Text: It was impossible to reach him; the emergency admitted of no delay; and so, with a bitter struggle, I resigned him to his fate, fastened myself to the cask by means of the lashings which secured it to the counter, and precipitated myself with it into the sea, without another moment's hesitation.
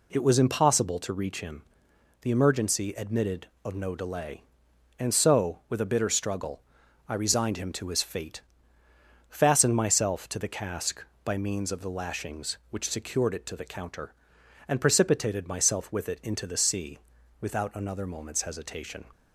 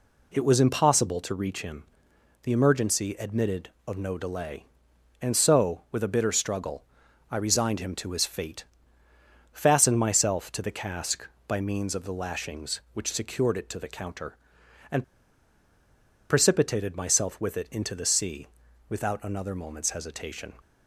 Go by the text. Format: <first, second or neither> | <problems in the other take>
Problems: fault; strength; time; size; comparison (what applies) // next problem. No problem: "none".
first | pauses between "and" and "precipitated"; strong; at 15.0 s; 1.2 s long